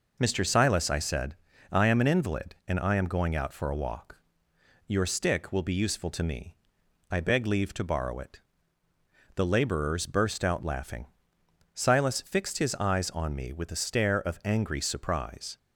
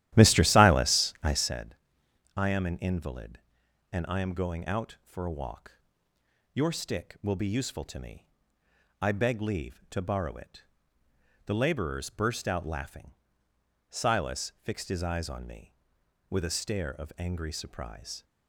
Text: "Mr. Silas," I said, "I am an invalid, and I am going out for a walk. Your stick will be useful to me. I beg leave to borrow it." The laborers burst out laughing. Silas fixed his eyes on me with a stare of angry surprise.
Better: first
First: none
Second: starts louder than the rest; strong; until 1.6 s; 13.5 dB

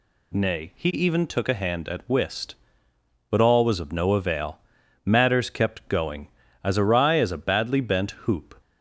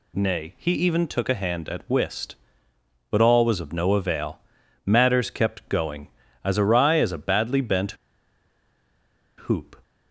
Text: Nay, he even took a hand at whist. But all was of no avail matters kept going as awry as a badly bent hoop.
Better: first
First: pauses between "avail" and "matters"; noticeable; at 4.5 s; 0.46 s long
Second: pauses between "avail" and "matters"; noticeable; at 4.3 s; 0.46 s long // pauses between "bent" and "hoop"; strong; at 7.9 s; 1.5 s long

